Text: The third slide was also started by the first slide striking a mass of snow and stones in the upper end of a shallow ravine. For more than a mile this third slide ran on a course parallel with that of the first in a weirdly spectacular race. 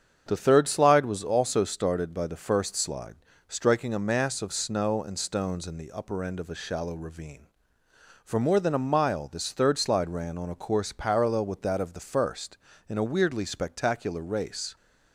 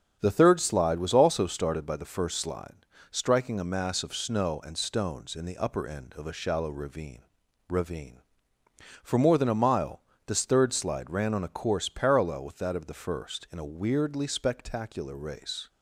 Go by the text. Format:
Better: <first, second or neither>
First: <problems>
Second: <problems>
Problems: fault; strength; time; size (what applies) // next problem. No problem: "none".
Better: first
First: starts louder than the rest; strong; until 1.2 s; 7.5 dB // pauses between "slide" and "striking"; slight; at 3.1 s; 0.32 s long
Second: starts louder than the rest; strong; until 1.2 s; 7.5 dB // pauses between "slide" and "striking"; slight; at 2.7 s; 0.36 s long // says "ravine" twice; at 7.6 s // pauses between "mile" and "this"; slight; at 10.0 s; 0.26 s long